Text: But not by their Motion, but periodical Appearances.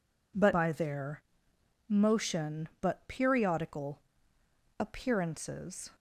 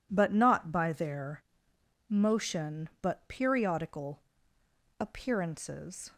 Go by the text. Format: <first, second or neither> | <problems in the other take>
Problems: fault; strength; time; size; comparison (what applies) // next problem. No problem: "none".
second | skips "not"; at 0.5 s // pauses between "their" and "Motion"; noticeable; at 1.2 s; 0.66 s long; noticeable in the second // pauses between "periodical" and "Appearances"; noticeable; at 4.0 s; 0.78 s long; noticeable in the second